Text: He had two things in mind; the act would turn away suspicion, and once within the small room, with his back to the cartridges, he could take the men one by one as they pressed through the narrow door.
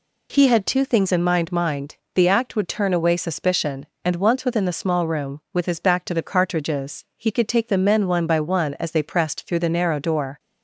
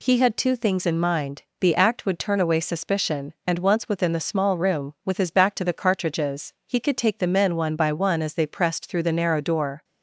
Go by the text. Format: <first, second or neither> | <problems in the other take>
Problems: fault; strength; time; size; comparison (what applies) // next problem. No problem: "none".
second | says "mind" twice; at 1.5 s